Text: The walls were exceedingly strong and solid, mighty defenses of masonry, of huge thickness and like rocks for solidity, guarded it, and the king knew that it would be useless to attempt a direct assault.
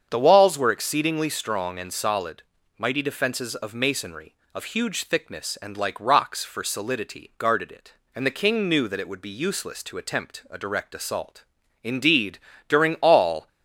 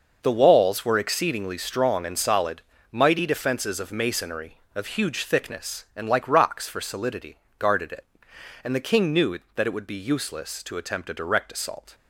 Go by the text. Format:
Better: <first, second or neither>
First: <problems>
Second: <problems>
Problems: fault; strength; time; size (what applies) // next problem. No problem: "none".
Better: second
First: starts louder than the rest; strong; until 1.1 s; 7.5 dB // goes on to say "Indeed during all"; from 11.8 s on; 1.6 s long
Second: none